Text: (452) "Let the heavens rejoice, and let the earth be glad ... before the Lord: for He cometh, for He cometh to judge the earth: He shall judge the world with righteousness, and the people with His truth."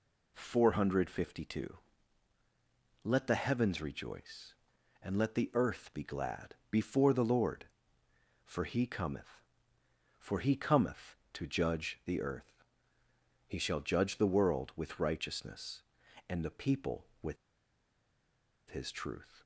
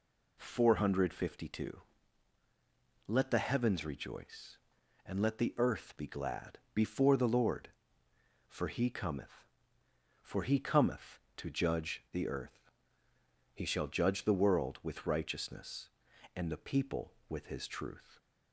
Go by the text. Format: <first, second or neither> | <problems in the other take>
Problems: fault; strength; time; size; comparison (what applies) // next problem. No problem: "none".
second | pauses between "with" and "His"; strong; at 17.3 s; 1.3 s long